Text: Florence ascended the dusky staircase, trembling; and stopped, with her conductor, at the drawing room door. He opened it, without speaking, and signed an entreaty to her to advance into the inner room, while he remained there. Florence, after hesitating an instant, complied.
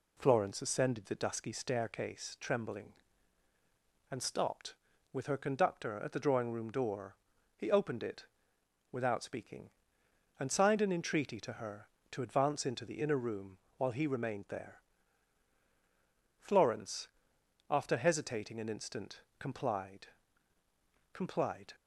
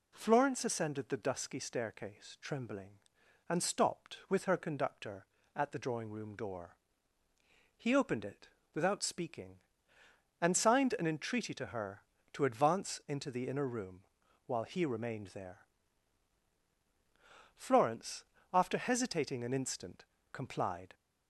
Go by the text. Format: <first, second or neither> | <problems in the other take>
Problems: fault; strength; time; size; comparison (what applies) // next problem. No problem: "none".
second | says "complied" twice; at 21.1 s